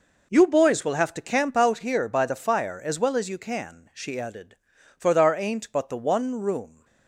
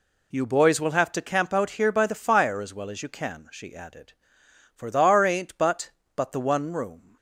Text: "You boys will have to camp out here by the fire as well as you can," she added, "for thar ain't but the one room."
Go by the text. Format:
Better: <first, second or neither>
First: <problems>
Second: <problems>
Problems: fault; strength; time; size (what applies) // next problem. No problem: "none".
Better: first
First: none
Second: says "but" twice; at 6.1 s